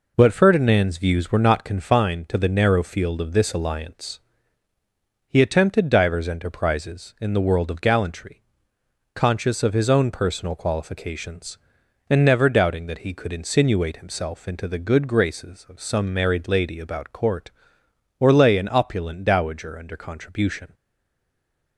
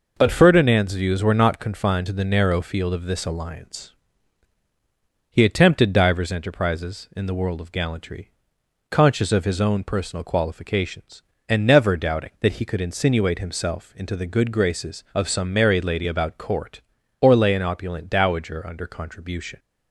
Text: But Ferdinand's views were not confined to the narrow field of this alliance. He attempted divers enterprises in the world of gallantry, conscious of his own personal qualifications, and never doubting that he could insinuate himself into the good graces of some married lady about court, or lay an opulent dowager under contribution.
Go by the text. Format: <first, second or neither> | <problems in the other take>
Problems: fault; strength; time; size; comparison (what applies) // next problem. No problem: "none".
second | stays silent after the last word; from 20.7 s on; 1.0 s long